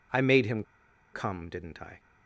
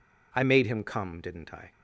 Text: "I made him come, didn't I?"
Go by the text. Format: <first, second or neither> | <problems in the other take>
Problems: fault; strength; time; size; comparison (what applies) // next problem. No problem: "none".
second | pauses between "him" and "come"; noticeable; at 0.6 s; 0.50 s long